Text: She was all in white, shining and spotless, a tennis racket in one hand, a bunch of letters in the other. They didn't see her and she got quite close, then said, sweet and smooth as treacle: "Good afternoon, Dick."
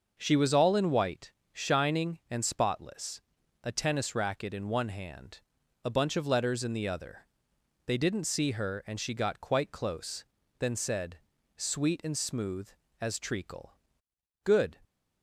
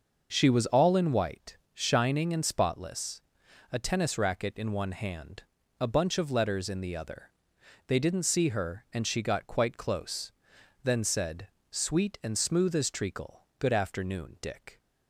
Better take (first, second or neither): second